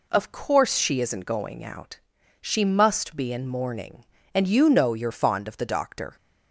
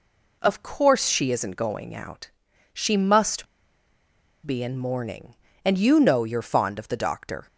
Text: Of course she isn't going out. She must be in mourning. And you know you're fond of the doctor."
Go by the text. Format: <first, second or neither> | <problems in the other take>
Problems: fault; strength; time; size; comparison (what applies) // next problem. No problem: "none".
first | pauses between "must" and "be"; at 3.4 s; 1.0 s long